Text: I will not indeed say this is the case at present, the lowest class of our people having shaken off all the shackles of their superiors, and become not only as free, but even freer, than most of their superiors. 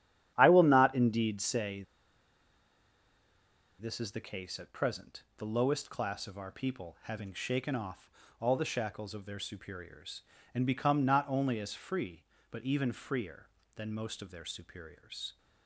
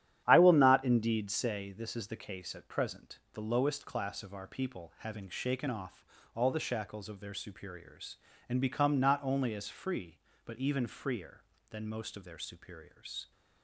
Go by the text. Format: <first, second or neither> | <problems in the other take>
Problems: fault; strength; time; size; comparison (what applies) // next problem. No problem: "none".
second | starts louder than the rest; strong; until 1.3 s; 10.5 dB; strong in the second // pauses between "say" and "this"; strong; at 1.8 s; 1.9 s long // pauses between "off" and "all"; slight; at 8.0 s; 0.32 s long; slight in the second